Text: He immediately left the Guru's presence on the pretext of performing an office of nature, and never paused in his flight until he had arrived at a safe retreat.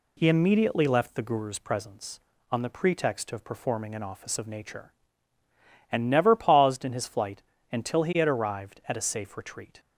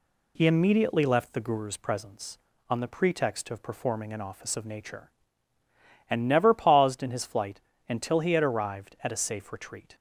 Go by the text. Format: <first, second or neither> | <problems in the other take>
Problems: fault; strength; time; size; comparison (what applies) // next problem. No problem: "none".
neither | pauses between "flight" and "until"; slight; the same in both